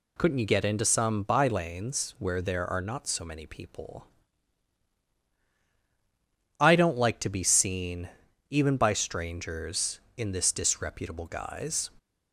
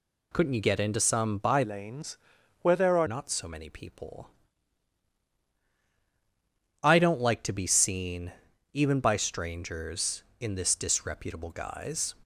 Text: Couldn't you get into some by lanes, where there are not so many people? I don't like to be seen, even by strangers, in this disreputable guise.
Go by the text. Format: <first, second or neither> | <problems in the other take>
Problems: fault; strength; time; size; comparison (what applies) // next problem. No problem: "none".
first | changes voice from "lanes" to "are"; from 1.6 to 3.0 s; 1.4 s long